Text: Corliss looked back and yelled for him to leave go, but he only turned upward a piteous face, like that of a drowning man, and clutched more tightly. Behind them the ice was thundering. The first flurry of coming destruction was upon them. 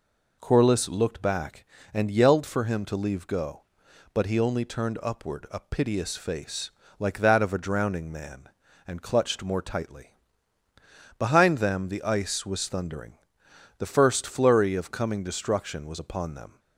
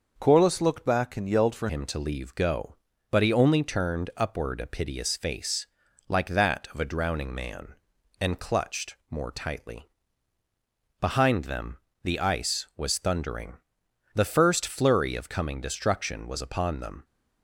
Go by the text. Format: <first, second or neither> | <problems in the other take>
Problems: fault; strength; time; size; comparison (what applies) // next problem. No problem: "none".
first | changes voice at "him"; from 1.6 s on; 15.4 s long // pauses between "them" and "the"; slight; at 11.7 s; 0.24 s long